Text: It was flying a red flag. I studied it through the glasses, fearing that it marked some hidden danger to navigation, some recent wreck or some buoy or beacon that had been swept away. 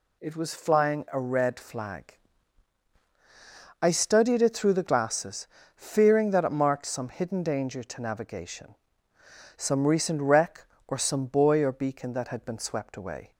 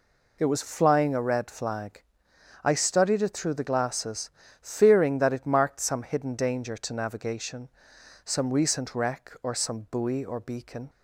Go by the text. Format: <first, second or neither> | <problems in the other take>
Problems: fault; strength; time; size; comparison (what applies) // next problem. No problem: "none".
first | stops before "that had been swept away"; at 10.8 s